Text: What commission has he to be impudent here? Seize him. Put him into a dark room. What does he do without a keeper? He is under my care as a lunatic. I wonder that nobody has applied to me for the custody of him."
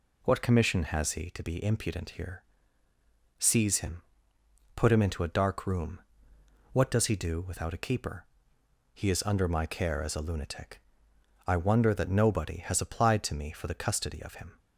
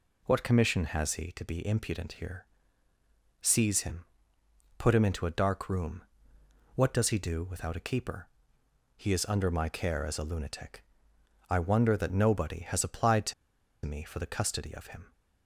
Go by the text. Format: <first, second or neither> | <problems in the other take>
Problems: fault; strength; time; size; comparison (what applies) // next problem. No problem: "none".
first | pauses between "to" and "me"; noticeable; at 13.3 s; 0.52 s long